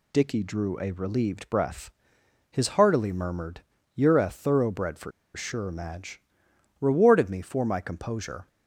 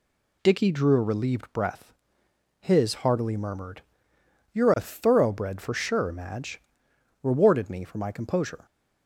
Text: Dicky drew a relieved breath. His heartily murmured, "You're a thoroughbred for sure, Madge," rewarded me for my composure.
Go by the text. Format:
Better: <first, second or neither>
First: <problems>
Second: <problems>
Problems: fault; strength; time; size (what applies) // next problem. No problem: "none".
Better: second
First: pauses between "for" and "sure"; slight; at 5.1 s; 0.24 s long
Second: none